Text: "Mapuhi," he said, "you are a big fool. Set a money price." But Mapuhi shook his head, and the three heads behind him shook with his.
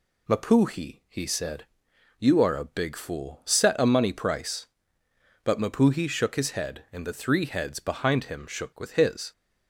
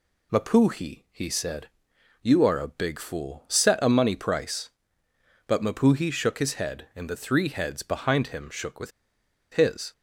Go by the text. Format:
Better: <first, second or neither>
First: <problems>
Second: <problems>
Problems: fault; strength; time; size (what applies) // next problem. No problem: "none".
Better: first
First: none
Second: pauses between "with" and "his"; noticeable; at 8.9 s; 0.61 s long